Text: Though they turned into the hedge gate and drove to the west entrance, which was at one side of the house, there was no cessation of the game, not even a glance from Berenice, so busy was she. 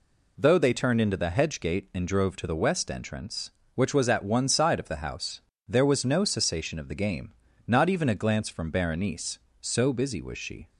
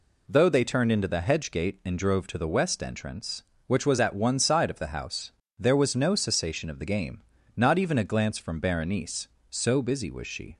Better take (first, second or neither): neither